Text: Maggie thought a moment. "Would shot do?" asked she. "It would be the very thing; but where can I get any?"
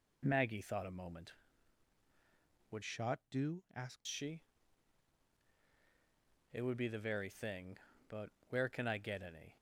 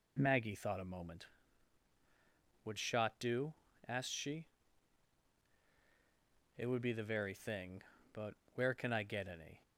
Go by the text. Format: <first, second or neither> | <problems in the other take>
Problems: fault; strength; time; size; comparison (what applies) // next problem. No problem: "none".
second | changes voice from "shot" to "asked"; from 2.8 to 4.0 s; 1.2 s long // pauses between "but" and "where"; slight; at 8.2 s; 0.22 s long; slight in the second